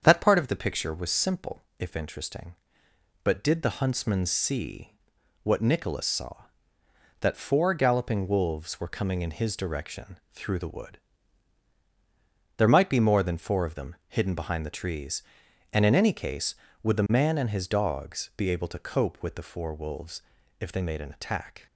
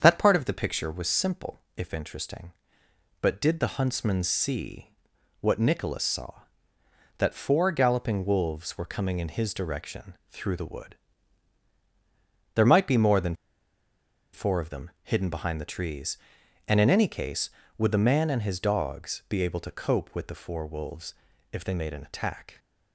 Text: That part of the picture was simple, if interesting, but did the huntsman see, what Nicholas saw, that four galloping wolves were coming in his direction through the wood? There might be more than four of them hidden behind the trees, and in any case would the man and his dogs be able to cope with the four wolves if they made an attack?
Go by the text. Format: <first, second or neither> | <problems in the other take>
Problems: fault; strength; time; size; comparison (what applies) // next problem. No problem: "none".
first | starts louder than the rest; strong; until 1.0 s; 7.5 dB; strong in the first // pauses between "direction" and "through"; slight; at 10.1 s; 0.16 s long; slight in the first // pauses between "than" and "four"; noticeable; at 13.3 s; 0.98 s long // pauses between "wolves" and "if"; at 21.1 s; 0.38 s long; also in the first